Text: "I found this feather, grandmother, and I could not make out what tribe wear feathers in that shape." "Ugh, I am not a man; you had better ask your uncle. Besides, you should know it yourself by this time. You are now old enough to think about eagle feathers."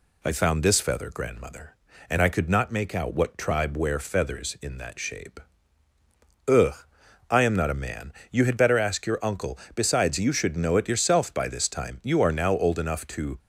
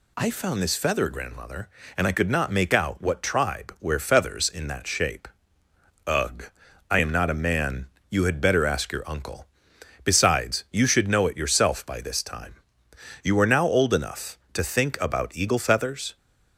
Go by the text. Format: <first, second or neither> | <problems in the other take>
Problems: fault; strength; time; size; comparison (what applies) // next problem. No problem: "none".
second | stops before "think about eagle feathers"; at 13.3 s